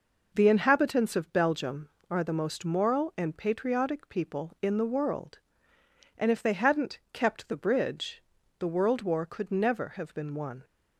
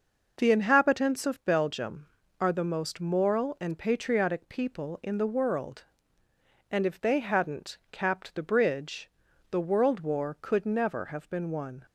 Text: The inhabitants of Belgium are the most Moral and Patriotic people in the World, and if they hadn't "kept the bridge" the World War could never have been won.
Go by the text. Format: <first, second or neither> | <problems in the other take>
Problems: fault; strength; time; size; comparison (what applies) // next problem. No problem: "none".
first | says "capped" for "kept"; at 7.9 s // pauses between "bridge" and "the"; at 9.1 s; 0.40 s long; slight in the first